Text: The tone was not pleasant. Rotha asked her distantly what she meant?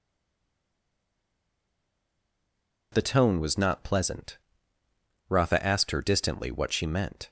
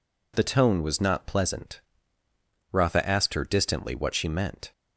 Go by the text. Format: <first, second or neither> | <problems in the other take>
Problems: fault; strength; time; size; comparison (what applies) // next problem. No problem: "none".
second | stays silent before the first word; strong; until 2.9 s; 2.9 s long